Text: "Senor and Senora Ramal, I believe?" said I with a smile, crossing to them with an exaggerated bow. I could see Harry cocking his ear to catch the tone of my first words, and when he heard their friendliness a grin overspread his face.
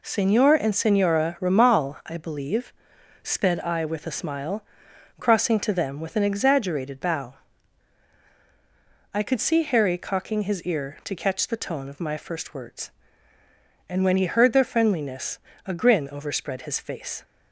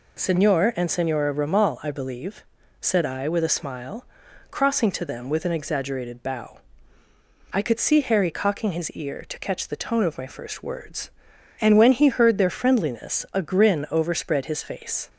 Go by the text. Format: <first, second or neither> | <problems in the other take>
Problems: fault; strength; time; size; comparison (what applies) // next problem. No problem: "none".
second | says "sped" for "said"; at 3.2 s // pauses between "friendliness" and "a"; slight; at 15.3 s; 0.30 s long